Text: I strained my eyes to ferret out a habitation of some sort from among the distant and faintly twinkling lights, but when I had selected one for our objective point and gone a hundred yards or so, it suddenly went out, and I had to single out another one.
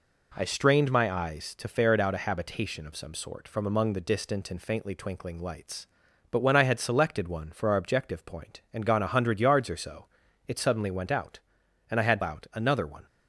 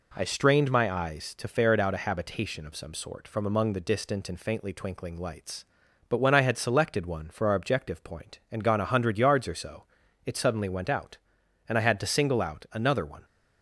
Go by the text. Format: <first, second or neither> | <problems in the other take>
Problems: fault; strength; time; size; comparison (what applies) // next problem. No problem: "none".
second | skips "to single"; at 12.2 s